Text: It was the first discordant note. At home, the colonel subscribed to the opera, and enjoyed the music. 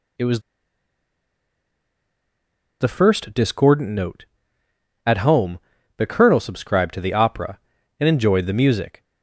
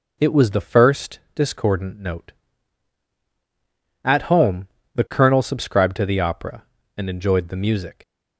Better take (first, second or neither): second